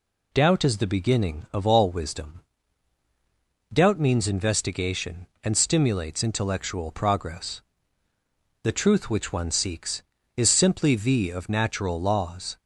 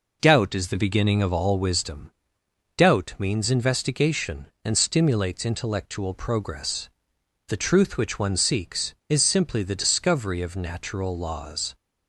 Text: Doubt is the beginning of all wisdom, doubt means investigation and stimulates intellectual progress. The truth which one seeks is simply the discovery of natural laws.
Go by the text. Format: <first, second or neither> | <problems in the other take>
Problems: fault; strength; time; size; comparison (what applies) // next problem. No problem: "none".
second | skips "discovery"; at 11.3 s